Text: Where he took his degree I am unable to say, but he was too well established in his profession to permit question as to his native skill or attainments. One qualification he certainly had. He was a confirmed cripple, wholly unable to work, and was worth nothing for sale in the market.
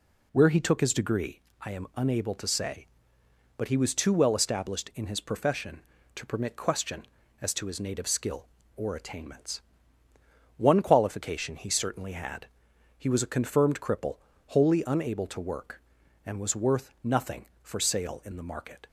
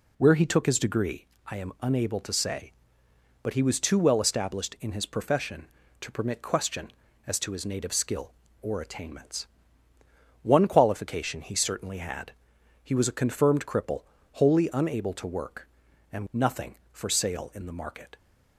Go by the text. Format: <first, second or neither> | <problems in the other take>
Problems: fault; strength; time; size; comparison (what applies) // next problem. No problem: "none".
first | pauses between "degree" and "I"; slight; at 1.2 s; 0.20 s long; slight in the first // skips "was worth"; at 16.2 s